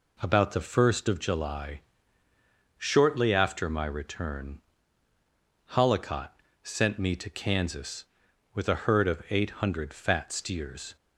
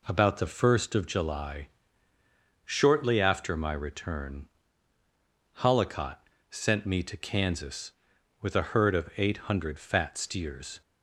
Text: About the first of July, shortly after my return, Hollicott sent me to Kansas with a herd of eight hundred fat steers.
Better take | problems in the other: neither | pauses between "Hollicott" and "sent"; slight; the same in both

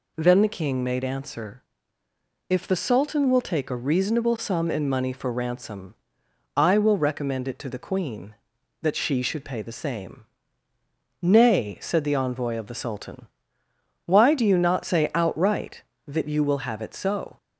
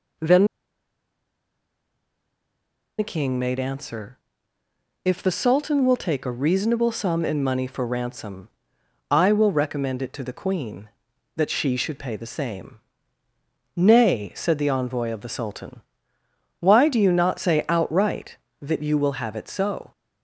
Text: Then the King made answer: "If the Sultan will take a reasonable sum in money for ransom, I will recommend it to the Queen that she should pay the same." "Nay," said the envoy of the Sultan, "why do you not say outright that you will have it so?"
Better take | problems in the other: first | pauses between "Then" and "the"; strong; at 0.4 s; 2.5 s long

